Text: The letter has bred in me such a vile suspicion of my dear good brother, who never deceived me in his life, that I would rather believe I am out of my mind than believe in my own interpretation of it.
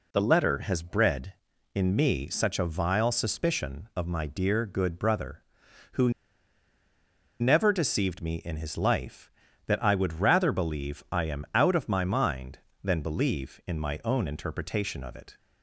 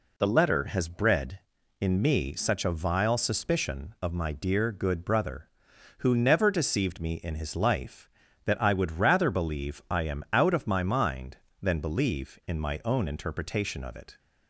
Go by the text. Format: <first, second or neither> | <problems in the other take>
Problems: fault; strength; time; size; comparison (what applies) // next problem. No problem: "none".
second | pauses between "who" and "never"; strong; at 6.1 s; 1.2 s long